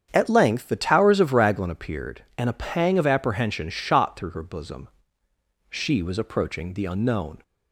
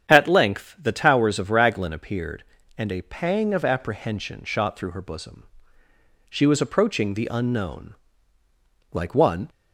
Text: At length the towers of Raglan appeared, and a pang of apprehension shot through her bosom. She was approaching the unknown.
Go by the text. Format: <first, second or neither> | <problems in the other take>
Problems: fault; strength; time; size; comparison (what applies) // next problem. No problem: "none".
first | starts louder than the rest; strong; until 1.1 s; 8.5 dB; strong in the first // goes on to say "Like one"; from 8.9 s on; 0.56 s long